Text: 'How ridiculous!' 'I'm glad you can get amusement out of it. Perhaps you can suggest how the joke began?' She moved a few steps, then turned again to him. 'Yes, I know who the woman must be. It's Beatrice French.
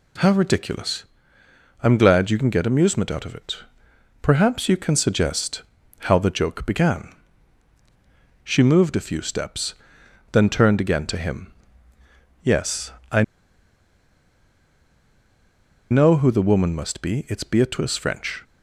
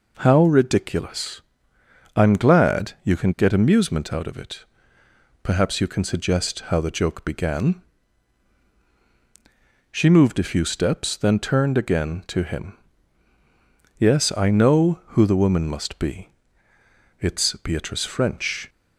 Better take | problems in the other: second | pauses between "suggest" and "how"; at 5.6 s; 0.38 s long // pauses between "I" and "know"; strong; at 13.2 s; 2.6 s long

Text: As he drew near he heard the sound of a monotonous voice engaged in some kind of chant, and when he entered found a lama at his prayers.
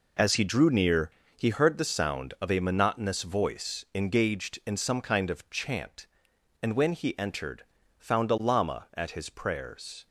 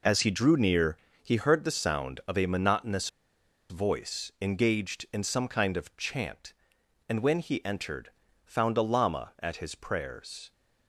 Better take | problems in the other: first | pauses between "near" and "he"; slight; at 0.9 s; 0.24 s long; slight in the first // pauses between "monotonous" and "voice"; noticeable; at 3.0 s; 0.61 s long // pauses between "entered" and "found"; at 8.0 s; 0.38 s long; also in the first

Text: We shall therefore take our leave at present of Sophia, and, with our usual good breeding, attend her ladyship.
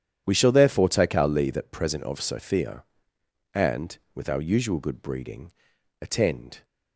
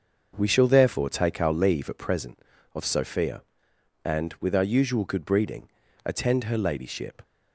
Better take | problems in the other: second | starts louder than the rest; strong; until 1.2 s; 10 dB; noticeable in the second // stops before "her ladyship"; at 6.6 s

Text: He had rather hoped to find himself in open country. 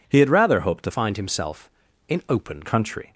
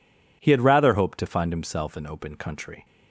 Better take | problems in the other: second | changes voice from "find" to "open"; from 0.9 to 2.6 s; 1.7 s long

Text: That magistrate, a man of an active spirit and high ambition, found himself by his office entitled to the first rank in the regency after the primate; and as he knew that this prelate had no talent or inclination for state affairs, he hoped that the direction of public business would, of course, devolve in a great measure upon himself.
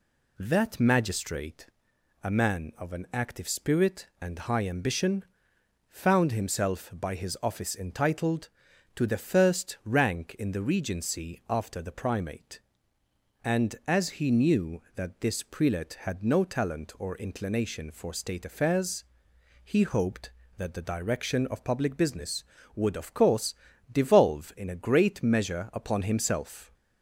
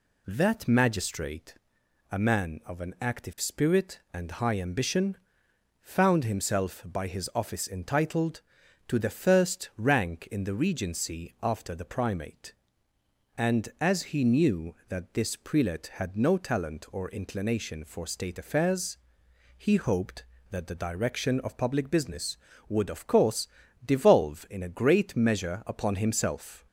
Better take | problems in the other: neither | none

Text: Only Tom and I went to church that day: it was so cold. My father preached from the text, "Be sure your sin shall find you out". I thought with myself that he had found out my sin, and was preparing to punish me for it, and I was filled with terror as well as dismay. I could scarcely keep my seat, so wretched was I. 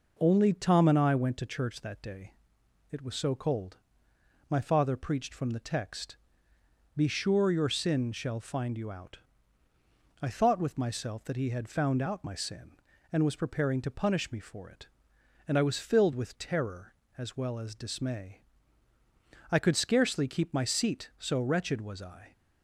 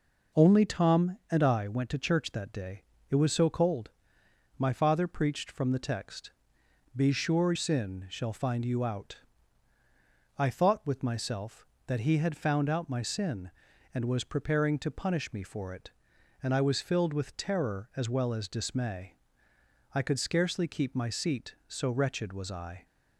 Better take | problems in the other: first | skips "your"; at 7.5 s

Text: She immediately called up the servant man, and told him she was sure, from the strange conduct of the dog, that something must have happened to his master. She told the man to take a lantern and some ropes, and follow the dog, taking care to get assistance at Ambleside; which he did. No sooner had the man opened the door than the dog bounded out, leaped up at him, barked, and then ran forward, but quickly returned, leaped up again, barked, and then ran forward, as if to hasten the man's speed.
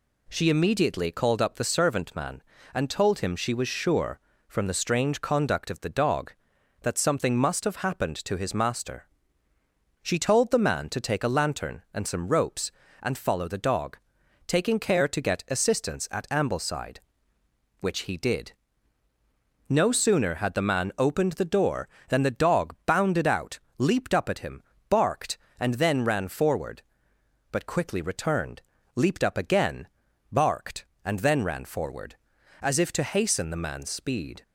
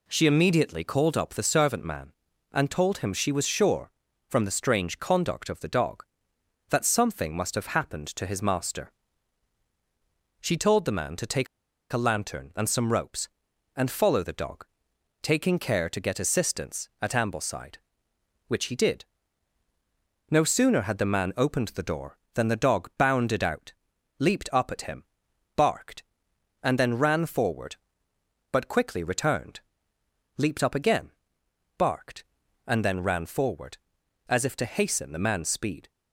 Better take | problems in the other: first | pauses between "take" and "a"; at 11.4 s; 0.45 s long

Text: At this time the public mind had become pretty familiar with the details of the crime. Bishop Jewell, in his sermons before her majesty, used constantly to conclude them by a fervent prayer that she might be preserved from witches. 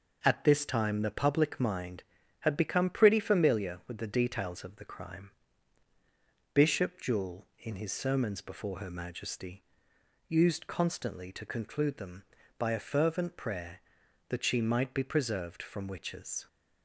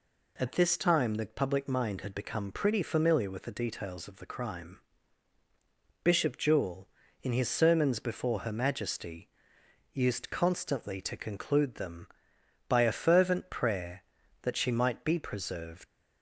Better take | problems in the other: first | stops before "from witches"; at 15.8 s

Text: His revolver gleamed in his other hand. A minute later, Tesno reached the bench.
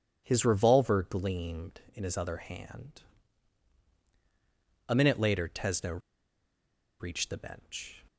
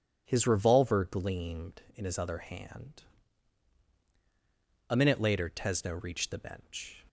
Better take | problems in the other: second | pauses between "Tesno" and "reached"; at 6.0 s; 1.0 s long

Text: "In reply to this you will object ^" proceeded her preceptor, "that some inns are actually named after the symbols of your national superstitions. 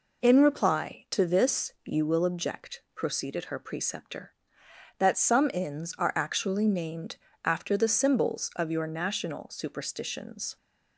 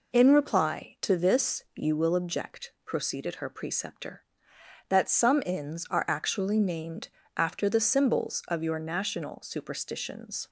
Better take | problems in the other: neither | pauses between "named" and "after"; slight; the same in both

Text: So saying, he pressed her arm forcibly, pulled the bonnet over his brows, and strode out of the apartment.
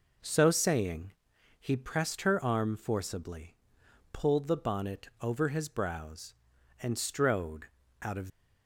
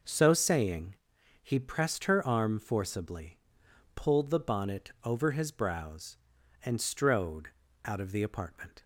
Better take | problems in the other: second | pauses between "strode" and "out"; slight; at 7.6 s; 0.36 s long; slight in the second // stops before "the apartment"; at 8.2 s

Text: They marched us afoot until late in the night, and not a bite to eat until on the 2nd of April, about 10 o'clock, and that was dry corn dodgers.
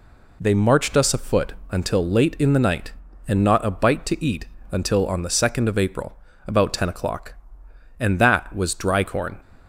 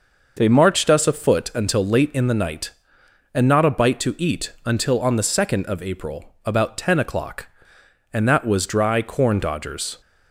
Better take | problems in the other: second | pauses between "afoot" and "until"; slight; at 1.5 s; 0.18 s long // pauses between "eat" and "until"; slight; at 4.4 s; 0.26 s long // stops before "dodgers"; at 9.4 s

